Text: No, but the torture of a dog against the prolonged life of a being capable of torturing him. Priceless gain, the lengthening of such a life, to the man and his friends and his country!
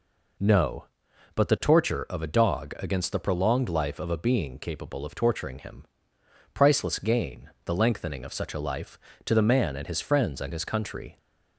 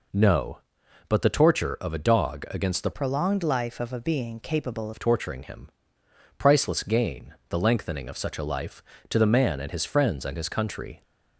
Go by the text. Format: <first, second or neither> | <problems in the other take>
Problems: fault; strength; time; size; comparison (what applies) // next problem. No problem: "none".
first | changes voice from "prolonged" to "capable"; from 2.9 to 4.9 s; 2.0 s long